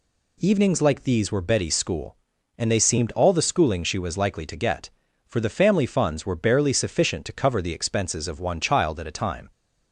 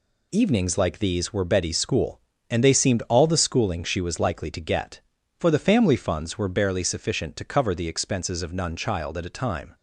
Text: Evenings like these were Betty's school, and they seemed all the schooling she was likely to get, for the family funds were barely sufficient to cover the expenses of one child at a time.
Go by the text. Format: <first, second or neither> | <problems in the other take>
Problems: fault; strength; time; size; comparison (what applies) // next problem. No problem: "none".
first | says "none" for "one"; at 8.5 s